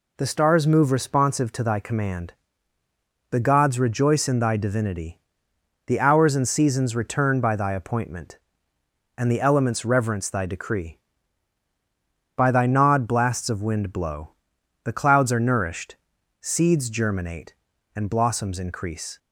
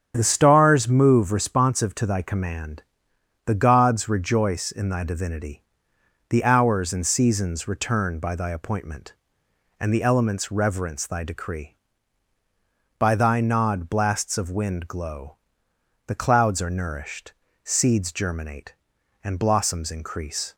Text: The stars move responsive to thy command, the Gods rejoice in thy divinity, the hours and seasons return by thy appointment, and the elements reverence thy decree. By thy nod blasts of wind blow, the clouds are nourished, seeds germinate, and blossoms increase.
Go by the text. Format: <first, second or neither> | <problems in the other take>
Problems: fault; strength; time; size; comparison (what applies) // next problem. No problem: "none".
first | starts louder than the rest; strong; until 1.1 s; 7.5 dB // says "glow" for "blow"; at 14.8 s